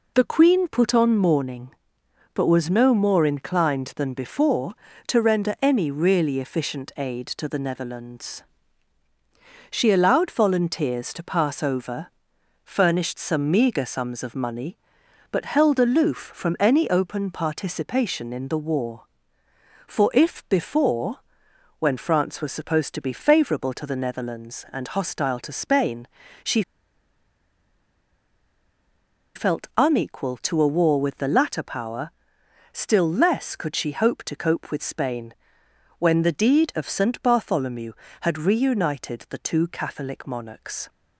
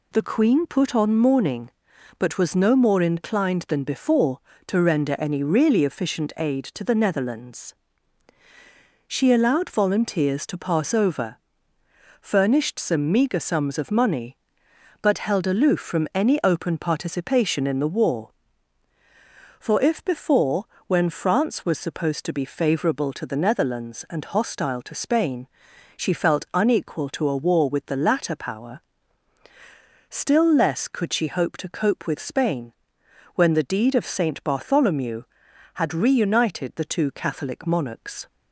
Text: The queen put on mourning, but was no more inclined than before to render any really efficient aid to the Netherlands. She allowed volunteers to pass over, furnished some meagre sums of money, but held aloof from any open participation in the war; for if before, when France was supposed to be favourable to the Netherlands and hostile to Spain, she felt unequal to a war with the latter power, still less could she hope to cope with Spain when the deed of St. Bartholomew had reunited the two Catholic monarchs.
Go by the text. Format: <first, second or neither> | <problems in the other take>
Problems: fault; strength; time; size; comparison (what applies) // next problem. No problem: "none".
second | pauses between "she" and "felt"; strong; at 26.6 s; 2.7 s long // pauses between "Spain" and "when"; noticeable; at 35.3 s; 0.66 s long; noticeable in the second